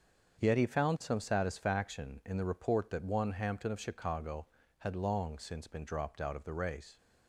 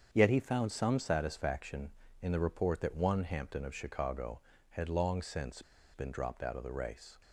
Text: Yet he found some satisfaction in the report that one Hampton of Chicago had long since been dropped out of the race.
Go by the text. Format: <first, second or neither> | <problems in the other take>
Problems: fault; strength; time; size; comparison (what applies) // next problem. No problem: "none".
first | starts louder than the rest; strong; until 1.1 s; 7.5 dB; also in the first // pauses between "since" and "been"; slight; at 5.6 s; 0.31 s long